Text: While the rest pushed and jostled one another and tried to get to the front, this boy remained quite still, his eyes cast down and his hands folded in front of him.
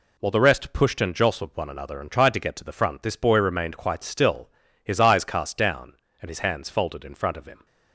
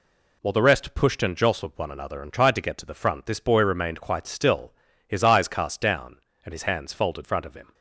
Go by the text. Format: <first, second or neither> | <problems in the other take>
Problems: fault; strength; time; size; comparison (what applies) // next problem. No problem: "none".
first | skips "in"; at 7.2 s